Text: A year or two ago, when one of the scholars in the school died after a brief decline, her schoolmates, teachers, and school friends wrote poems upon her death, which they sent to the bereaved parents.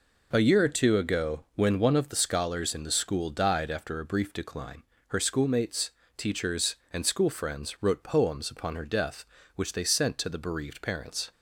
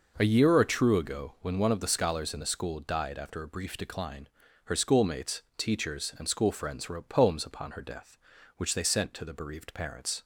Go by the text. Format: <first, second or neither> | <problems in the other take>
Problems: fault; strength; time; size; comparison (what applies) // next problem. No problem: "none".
first | says "true" for "two"; at 0.6 s